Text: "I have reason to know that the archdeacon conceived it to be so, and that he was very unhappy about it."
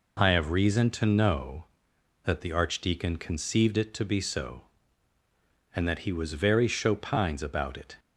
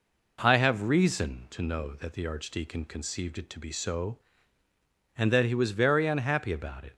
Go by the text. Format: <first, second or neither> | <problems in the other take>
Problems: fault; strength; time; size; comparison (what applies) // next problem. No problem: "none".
second | says "chopines" for "unhappy"; at 6.6 s